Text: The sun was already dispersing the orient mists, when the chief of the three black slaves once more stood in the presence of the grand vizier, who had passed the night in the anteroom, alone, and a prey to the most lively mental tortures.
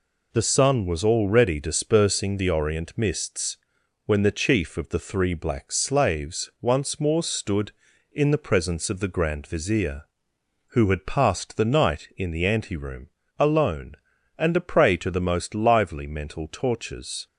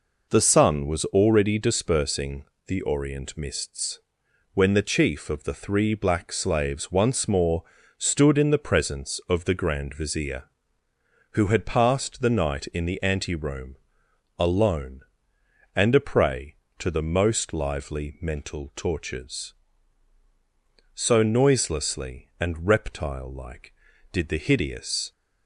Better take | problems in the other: first | pauses between "dispersing" and "the"; slight; at 2.4 s; 0.20 s long // pauses between "more" and "stood"; at 7.6 s; 0.38 s long // goes on to say "So noiselessly and reptile like did the hideous"; strong; from 20.9 s on; 4.1 s long

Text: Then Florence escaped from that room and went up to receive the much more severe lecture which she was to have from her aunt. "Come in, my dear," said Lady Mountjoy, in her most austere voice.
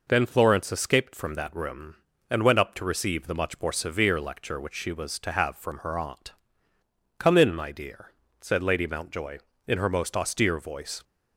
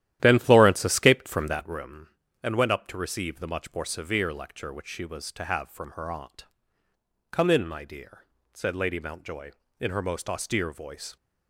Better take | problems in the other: first | starts louder than the rest; strong; until 1.8 s; 12.5 dB

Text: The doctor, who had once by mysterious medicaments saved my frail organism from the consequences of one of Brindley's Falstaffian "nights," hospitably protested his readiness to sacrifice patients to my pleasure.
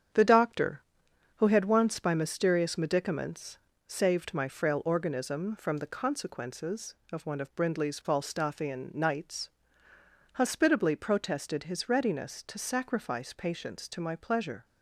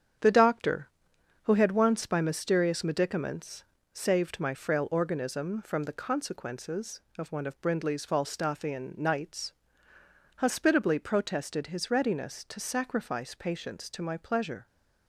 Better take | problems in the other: neither | starts louder than the rest; strong; the same in both // pauses between "medicaments" and "saved"; slight; the same in both

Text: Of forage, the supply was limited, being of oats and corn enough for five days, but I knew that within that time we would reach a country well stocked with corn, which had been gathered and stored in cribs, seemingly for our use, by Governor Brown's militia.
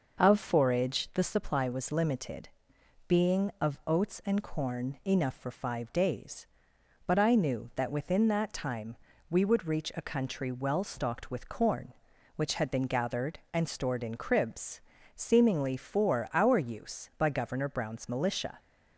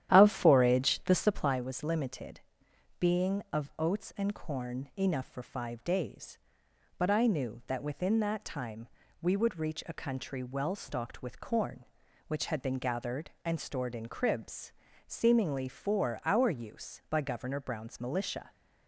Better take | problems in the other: first | starts louder than the rest; strong; until 1.6 s; 11.5 dB // pauses between "time" and "we"; slight; at 8.8 s; 0.34 s long; slight in the first

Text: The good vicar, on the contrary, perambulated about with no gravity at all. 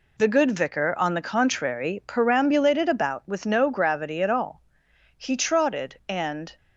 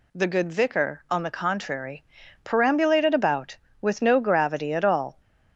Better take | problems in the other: second | goes on to say "He trotted and"; from 5.1 s on; 1.4 s long

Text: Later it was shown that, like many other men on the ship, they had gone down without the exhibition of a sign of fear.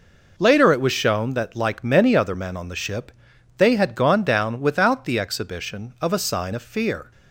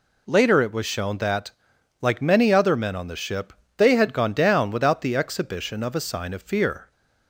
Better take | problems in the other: neither | none

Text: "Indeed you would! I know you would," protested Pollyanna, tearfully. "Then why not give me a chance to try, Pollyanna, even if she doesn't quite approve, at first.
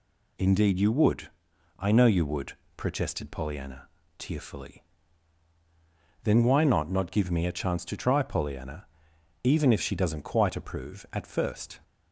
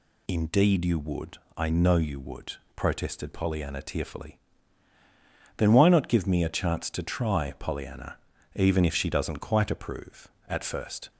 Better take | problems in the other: second | says "not" twice; at 6.9 s

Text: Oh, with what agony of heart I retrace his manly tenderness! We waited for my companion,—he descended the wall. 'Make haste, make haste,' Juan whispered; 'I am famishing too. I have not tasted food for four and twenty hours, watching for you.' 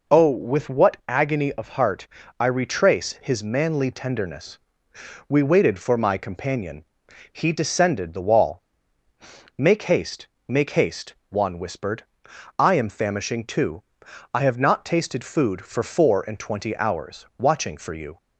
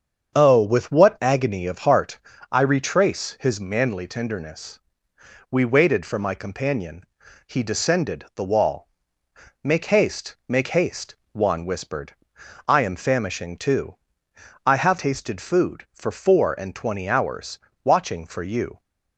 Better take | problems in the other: first | starts louder than the rest; until 1.4 s; 7 dB // pauses between "heart" and "I"; slight; at 2.1 s; 0.32 s long; slight in the first // skips "not"; at 14.9 s

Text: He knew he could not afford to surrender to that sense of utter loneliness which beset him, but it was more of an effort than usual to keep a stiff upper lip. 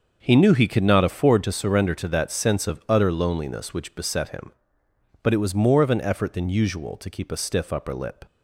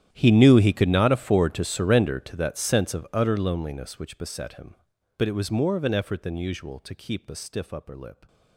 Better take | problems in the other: first | gets quieter; strong; throughout; 19.5 dB // starts louder than the rest; strong; until 1.1 s; 11 dB; also in the first

